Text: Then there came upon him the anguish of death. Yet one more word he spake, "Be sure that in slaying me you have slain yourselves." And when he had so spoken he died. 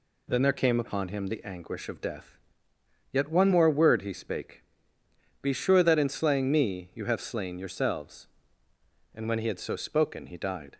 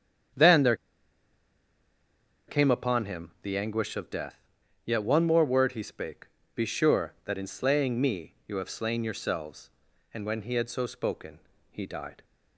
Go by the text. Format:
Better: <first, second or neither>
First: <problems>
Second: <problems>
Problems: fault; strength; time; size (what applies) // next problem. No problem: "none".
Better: first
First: none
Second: starts louder than the rest; strong; until 3.0 s; 8.5 dB // pauses between "there" and "came"; strong; at 0.7 s; 1.7 s long // pauses between "spoken" and "he"; slight; at 11.3 s; 0.32 s long